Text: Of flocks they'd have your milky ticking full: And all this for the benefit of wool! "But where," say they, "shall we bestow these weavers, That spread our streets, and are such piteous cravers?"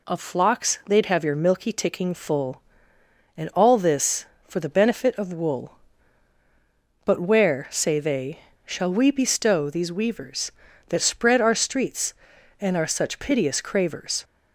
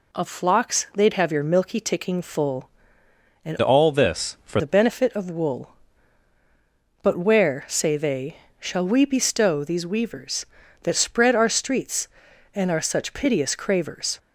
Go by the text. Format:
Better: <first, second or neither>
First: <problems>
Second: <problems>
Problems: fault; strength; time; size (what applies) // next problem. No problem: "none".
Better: first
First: none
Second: changes voice from "all" to "for"; from 3.6 to 4.6 s; 1.0 s long